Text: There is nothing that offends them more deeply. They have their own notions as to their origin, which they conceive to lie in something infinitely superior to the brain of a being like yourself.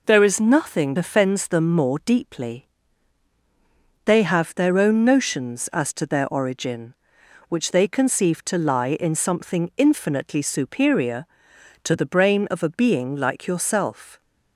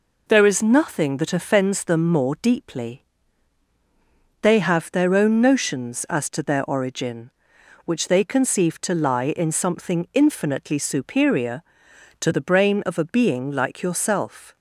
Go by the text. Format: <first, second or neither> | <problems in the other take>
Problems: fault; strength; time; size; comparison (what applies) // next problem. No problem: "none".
second | skips "that"; at 0.9 s